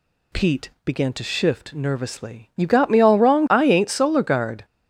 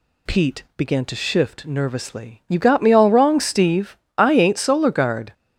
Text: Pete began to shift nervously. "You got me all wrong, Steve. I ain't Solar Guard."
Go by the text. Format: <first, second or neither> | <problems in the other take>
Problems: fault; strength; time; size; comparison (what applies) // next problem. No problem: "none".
second | skips "Steve"; at 3.4 s